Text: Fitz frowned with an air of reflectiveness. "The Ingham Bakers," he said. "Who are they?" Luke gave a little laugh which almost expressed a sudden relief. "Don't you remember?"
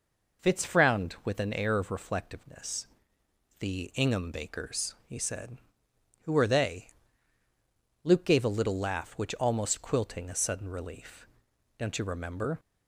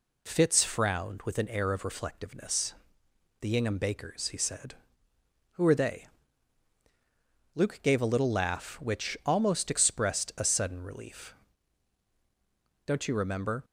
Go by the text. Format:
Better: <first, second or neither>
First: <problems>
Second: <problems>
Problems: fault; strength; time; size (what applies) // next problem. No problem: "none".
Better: second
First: says "quilting" for "expressed"; at 9.8 s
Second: none